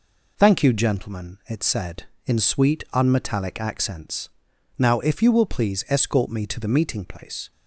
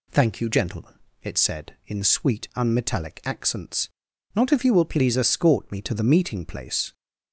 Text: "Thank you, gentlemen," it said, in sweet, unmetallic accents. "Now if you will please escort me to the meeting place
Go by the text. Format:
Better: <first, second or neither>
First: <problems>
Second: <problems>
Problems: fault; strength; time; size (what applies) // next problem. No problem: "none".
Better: first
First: none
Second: says "Not" for "Now"; at 4.3 s